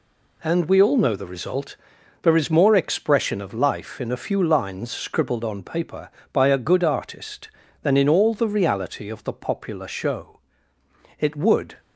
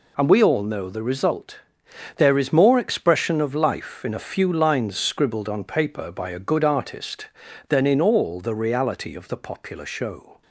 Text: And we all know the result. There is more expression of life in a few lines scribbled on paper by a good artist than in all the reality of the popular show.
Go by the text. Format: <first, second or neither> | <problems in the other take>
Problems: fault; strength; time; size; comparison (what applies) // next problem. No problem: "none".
second | goes on to say "It would"; from 11.1 s on; 0.60 s long